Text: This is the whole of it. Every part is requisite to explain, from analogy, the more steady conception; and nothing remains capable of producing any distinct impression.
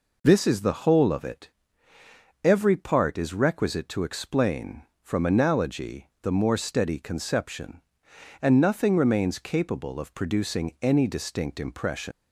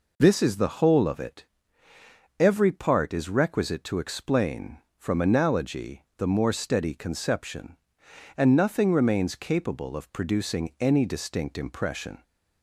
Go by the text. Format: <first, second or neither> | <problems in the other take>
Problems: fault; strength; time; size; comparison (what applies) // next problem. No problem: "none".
second | leaves "impression" unfinished; at 12.1 s; 130 ms